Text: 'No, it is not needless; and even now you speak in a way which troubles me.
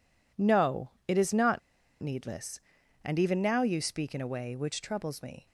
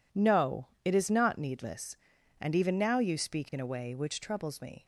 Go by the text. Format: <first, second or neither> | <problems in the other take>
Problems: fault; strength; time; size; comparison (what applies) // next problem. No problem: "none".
second | pauses between "not" and "needless"; at 1.5 s; 0.41 s long